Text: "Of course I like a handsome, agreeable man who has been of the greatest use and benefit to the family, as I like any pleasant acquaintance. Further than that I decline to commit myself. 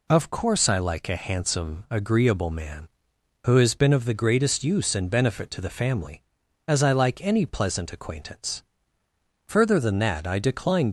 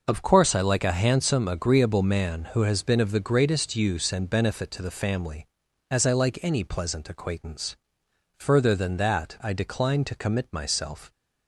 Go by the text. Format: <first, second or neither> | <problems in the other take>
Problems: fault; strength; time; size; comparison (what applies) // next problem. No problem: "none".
second | stops before "to commit myself"; at 10.8 s